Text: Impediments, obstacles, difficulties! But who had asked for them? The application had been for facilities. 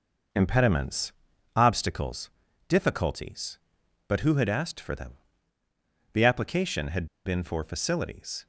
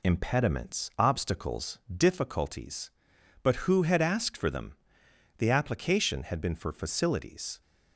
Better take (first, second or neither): second